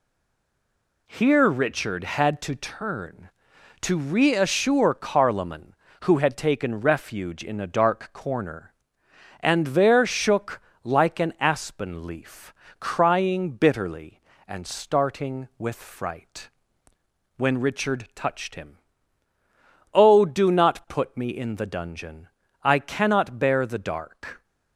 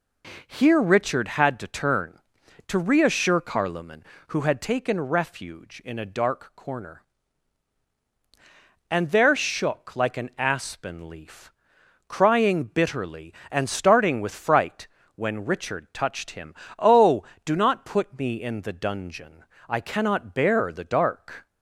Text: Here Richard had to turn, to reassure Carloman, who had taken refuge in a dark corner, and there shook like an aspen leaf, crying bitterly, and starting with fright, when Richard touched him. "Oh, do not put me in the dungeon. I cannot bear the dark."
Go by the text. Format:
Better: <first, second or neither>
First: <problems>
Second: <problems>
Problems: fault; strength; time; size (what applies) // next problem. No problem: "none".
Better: second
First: stays silent before the first word; until 1.0 s; 1.0 s long // pauses between "shook" and "like"; slight; at 10.6 s; 0.22 s long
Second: none